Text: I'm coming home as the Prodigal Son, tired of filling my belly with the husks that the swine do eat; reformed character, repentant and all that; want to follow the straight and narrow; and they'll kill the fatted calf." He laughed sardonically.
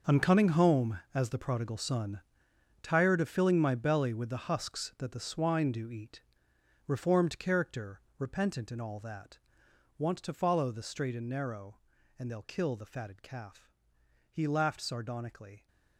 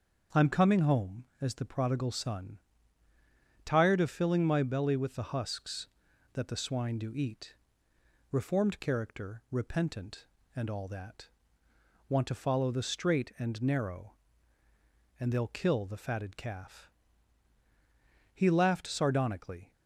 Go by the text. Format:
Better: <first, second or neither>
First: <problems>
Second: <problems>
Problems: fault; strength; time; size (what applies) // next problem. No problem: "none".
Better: second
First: gets quieter; strong; throughout; 14 dB // starts louder than the rest; noticeable; until 1.2 s; 6 dB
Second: starts louder than the rest; until 1.5 s; 7 dB